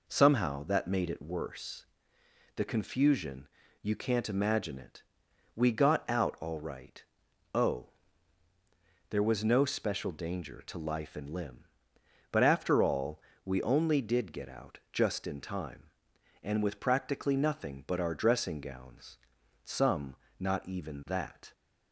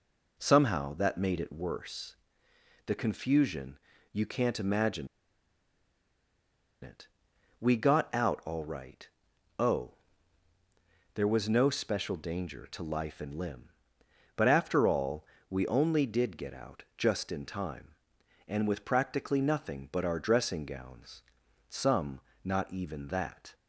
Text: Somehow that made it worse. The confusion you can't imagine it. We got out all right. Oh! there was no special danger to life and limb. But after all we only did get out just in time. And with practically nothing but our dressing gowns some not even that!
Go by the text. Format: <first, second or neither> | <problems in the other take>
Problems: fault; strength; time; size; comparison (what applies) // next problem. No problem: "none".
first | pauses between "confusion" and "you"; slight; at 3.7 s; 0.34 s long; slight in the first // pauses between "imagine" and "it"; strong; at 5.0 s; 1.7 s long // pauses between "all" and "we"; slight; at 15.2 s; 0.24 s long; slight in the first // pauses between "gowns" and "some"; noticeable; at 21.2 s; 0.46 s long; noticeable in the first // pauses between "some" and "not"; slight; at 22.1 s; 0.26 s long; slight in the first